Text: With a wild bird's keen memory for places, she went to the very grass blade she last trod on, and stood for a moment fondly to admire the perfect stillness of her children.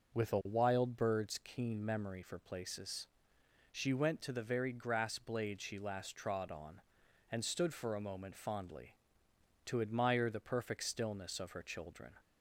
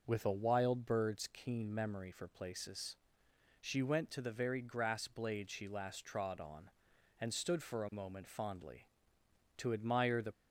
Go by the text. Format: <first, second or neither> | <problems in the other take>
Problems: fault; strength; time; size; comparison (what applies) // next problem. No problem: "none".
first | stops before "perfect stillness of her children"; at 10.3 s